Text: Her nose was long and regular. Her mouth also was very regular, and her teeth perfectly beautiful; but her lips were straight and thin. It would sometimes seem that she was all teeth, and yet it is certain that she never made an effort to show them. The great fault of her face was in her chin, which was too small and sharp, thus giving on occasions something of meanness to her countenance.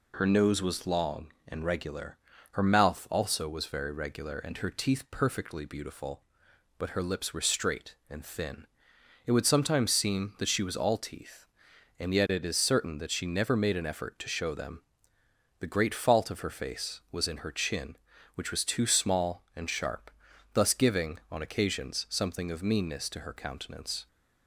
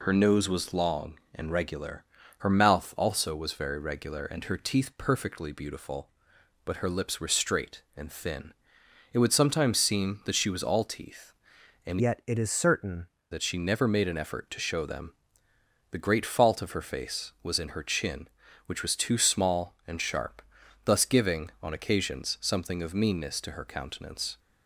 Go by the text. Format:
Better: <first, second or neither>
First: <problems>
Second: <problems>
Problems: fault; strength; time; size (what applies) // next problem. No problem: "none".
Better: first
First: none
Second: changes voice from "yet" to "certain"; from 11.9 to 13.0 s; 1.1 s long